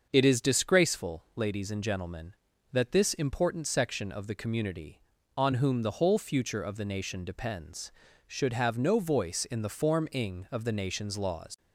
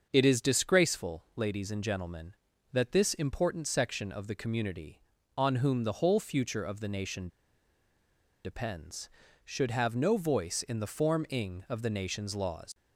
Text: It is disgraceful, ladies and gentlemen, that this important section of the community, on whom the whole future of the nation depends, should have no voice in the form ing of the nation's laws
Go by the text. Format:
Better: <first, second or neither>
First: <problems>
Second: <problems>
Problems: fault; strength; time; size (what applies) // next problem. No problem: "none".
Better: first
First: starts louder than the rest; until 1.1 s; 6.5 dB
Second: starts louder than the rest; until 1.1 s; 6.5 dB // pauses between "nation" and "depends"; at 7.2 s; 1.1 s long